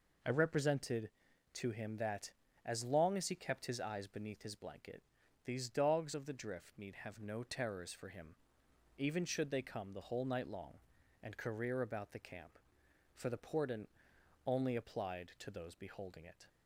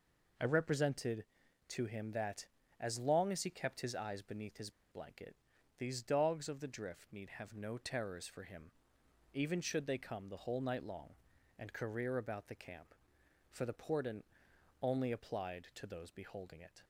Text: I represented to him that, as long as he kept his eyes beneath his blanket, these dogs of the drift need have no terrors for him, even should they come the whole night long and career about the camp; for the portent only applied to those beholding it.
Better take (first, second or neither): first